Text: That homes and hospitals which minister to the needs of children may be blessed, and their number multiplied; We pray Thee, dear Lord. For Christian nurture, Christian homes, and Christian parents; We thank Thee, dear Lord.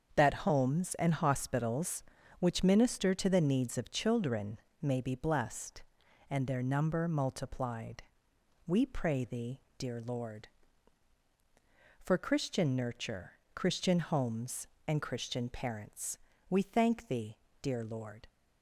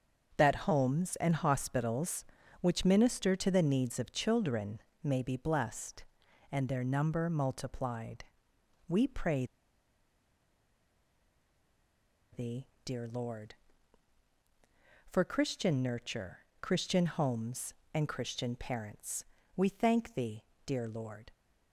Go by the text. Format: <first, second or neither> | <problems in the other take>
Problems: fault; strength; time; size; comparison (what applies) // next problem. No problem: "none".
first | starts louder than the rest; until 1.3 s; 7 dB; also in the first // pauses between "children" and "may"; slight; at 4.8 s; 0.24 s long; slight in the first // pauses between "pray" and "Thee"; strong; at 9.4 s; 2.8 s long